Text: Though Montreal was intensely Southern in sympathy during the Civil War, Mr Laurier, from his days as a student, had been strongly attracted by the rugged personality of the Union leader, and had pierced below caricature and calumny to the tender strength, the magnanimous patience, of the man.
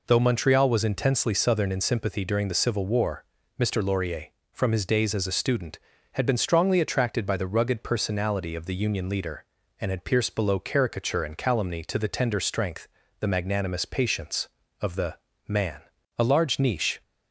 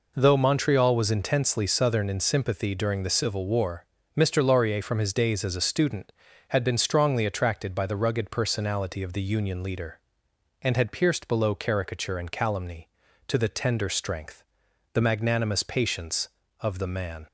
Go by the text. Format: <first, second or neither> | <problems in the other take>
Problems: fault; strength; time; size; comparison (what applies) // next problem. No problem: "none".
second | pauses between "the" and "man"; slight; at 15.1 s; 0.32 s long // goes on to say "A large niche"; noticeable; from 16.1 s on; 0.84 s long